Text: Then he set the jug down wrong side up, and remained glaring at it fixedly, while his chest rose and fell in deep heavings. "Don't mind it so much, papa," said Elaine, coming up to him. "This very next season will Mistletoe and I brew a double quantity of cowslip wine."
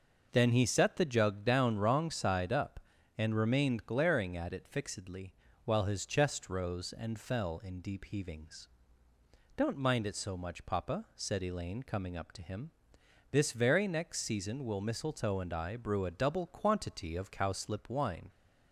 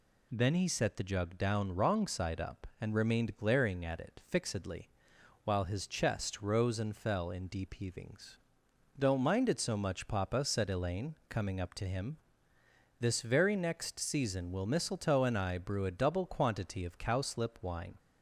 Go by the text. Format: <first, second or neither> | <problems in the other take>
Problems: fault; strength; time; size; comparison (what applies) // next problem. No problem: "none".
neither | none